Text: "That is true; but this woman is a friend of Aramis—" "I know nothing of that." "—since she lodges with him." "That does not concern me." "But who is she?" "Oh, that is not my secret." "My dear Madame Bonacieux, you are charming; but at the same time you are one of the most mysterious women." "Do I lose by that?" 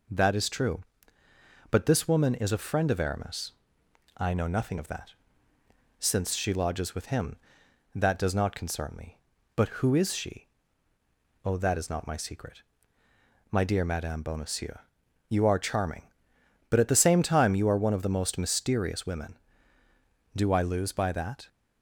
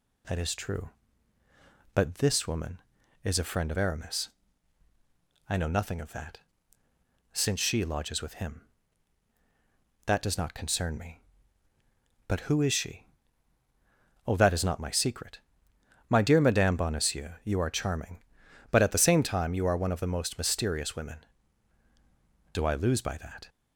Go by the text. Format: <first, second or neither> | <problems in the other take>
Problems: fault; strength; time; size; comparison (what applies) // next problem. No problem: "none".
neither | none